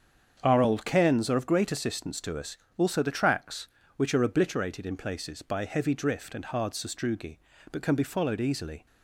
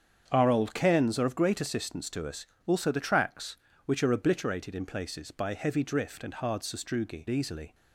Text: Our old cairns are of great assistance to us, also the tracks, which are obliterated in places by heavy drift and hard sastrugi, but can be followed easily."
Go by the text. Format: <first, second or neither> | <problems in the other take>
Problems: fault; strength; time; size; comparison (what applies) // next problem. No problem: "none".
first | starts louder than the rest; strong; until 1.3 s; 7.5 dB; strong in the first // skips "but can be followed"; at 7.2 s